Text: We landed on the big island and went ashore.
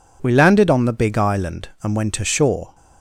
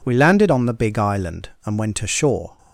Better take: neither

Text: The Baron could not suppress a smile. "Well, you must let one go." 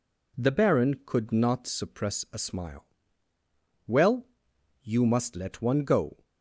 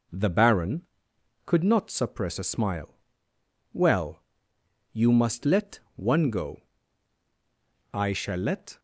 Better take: first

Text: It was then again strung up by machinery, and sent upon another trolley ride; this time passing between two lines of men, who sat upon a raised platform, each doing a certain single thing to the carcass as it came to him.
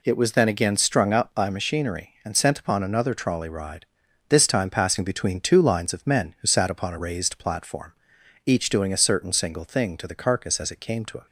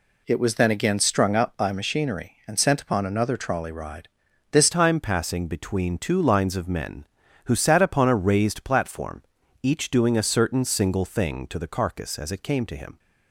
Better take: first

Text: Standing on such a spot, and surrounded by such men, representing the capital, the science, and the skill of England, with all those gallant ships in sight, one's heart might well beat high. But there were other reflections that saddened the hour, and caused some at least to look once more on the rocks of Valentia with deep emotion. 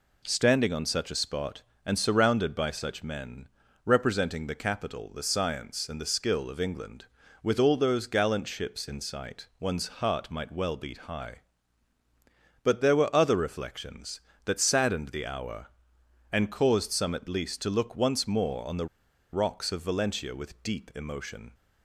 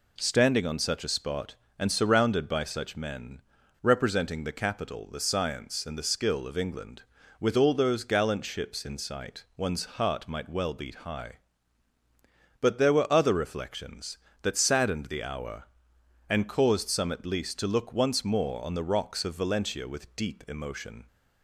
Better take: second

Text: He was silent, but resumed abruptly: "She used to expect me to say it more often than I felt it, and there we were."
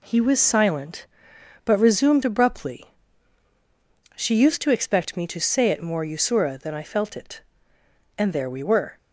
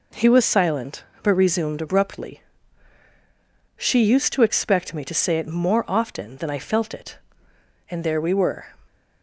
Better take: second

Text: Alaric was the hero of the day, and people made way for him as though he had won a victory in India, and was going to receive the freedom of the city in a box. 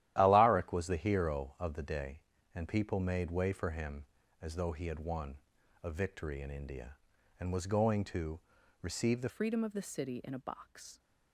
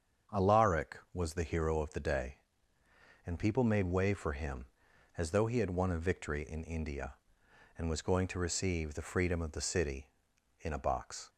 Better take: second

